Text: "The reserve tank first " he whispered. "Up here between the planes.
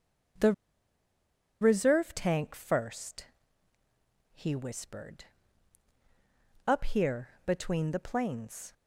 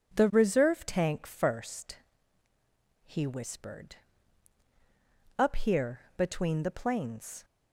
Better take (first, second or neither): second